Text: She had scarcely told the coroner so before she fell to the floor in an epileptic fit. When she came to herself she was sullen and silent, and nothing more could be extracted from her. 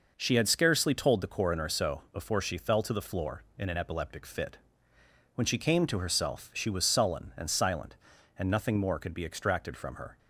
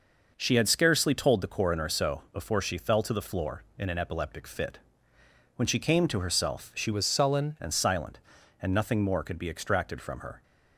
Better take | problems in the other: first | changes voice from "was" to "sullen"; from 6.9 to 7.5 s; 0.6 s long

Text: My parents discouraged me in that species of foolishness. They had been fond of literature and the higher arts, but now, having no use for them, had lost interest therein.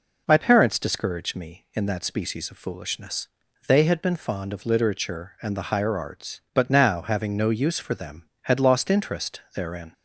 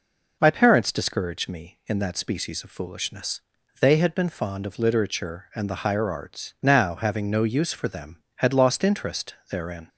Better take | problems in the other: first | skips "but"; at 6.5 s // pauses between "interest" and "therein"; slight; at 9.3 s; 0.16 s long

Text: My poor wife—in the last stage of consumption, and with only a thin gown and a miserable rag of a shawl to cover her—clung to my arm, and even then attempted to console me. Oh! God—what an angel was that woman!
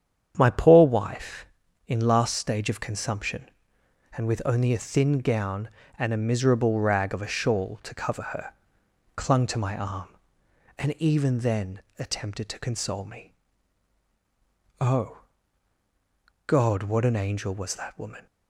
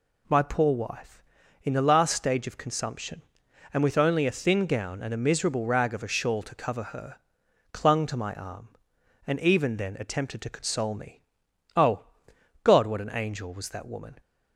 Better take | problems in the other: second | starts louder than the rest; strong; until 1.3 s; 8.5 dB // skips "the"; at 2.0 s // pauses between "then" and "attempted"; slight; at 11.7 s; 0.18 s long

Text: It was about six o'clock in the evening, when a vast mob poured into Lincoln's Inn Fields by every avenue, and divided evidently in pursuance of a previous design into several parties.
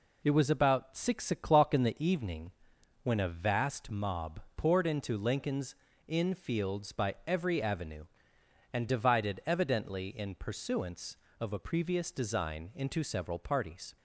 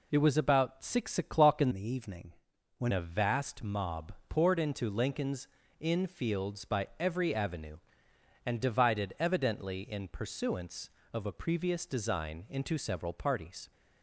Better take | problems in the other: first | changes voice from "the" to "when"; from 1.7 to 2.9 s; 1.2 s long // pauses between "mob" and "poured"; slight; at 4.1 s; 0.16 s long; slight in the first // pauses between "Lincoln's" and "Inn"; slight; at 5.4 s; 0.34 s long; slight in the first

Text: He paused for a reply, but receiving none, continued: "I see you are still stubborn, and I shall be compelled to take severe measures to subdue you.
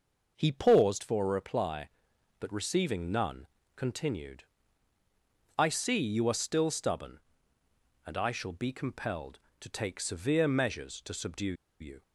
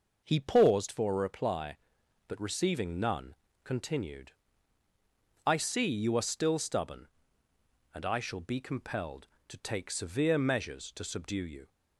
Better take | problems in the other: second | pauses between "subdue" and "you"; slight; at 11.5 s; 0.26 s long

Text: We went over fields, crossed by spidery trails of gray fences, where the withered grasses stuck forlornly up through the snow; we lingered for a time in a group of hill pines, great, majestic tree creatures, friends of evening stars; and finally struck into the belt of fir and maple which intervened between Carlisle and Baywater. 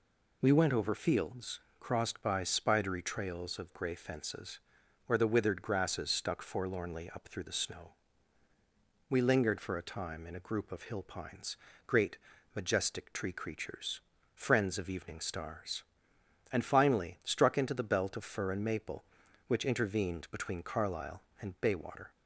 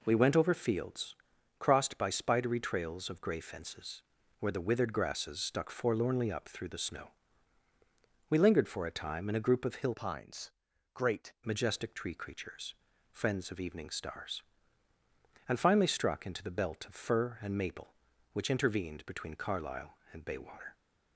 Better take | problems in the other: first | changes voice from "pines" to "great"; from 9.9 to 11.3 s; 1.4 s long

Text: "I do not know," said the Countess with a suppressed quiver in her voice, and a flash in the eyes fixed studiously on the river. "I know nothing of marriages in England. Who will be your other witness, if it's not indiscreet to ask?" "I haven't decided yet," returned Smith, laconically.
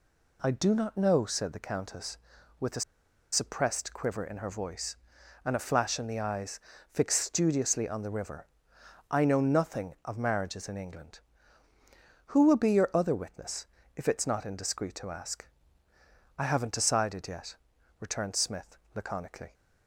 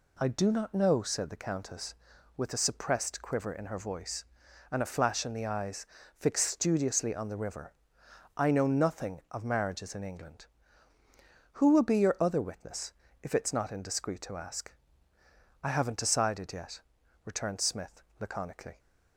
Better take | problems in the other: second | pauses between "a" and "suppressed"; noticeable; at 2.8 s; 0.51 s long // pauses between "eyes" and "fixed"; slight; at 6.5 s; 0.32 s long; slight in the second

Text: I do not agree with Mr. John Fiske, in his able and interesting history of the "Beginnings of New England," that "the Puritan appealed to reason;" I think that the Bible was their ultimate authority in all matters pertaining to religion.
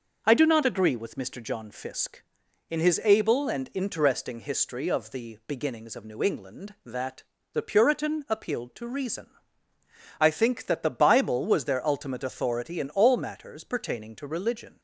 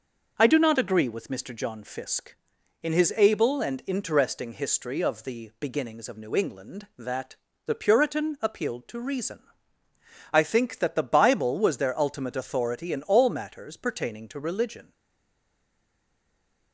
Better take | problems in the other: first | pauses between "that" and "the"; slight; at 7.3 s; 0.30 s long; slight in the first // stays silent after the last word; noticeable; from 14.9 s on; 1.8 s long

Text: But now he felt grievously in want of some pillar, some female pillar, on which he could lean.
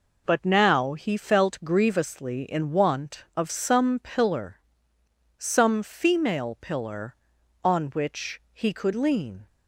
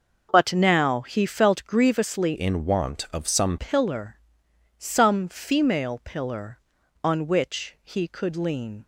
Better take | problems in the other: first | changes voice from "in" to "some"; from 2.3 to 3.5 s; 1.2 s long

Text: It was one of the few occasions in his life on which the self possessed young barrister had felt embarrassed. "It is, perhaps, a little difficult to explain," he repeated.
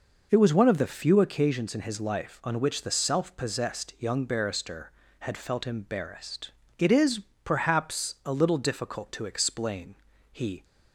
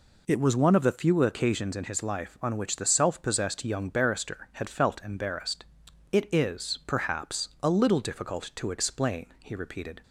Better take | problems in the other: second | stops before "repeated"; at 10.6 s

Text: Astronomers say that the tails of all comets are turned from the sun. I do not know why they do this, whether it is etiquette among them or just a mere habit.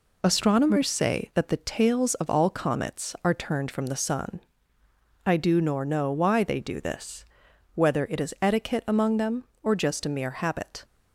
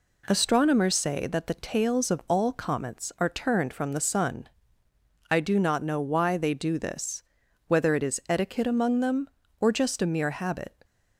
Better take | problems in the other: second | says "nor" for "not"; at 5.5 s

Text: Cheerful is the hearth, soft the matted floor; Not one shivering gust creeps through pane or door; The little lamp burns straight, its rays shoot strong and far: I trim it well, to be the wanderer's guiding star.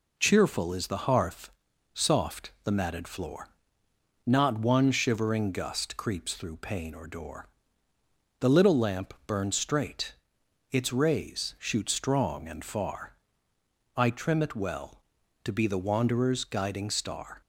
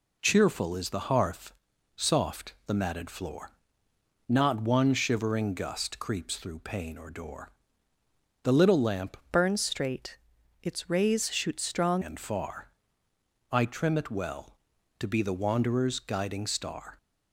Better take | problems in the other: first | changes voice from "burns" to "strong"; from 9.3 to 12.0 s; 2.7 s long

